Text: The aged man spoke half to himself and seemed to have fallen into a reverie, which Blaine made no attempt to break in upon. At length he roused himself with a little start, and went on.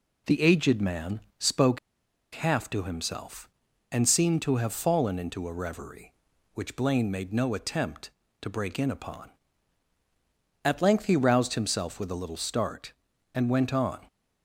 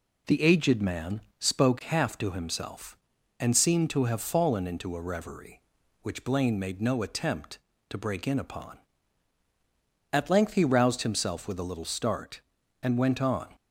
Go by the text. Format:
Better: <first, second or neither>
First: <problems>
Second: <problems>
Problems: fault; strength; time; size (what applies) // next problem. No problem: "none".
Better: second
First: pauses between "man" and "spoke"; slight; at 1.1 s; 0.20 s long // pauses between "spoke" and "half"; noticeable; at 1.7 s; 0.55 s long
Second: pauses between "man" and "spoke"; slight; at 1.1 s; 0.20 s long